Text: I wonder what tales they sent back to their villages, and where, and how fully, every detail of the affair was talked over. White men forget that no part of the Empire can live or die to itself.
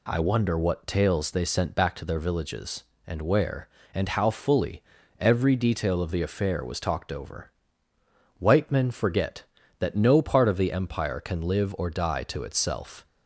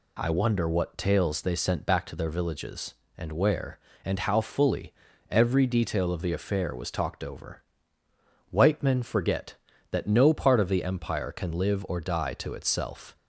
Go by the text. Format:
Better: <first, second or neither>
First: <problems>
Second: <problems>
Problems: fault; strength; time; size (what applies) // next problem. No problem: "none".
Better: neither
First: none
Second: none